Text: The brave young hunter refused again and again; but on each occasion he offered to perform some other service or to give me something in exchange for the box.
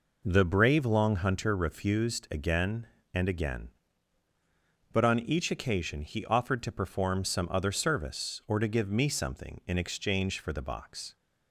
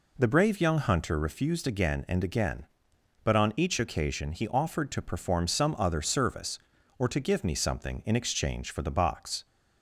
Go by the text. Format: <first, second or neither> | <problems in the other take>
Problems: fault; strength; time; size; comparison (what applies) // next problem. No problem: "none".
second | says "long" for "young"; at 0.8 s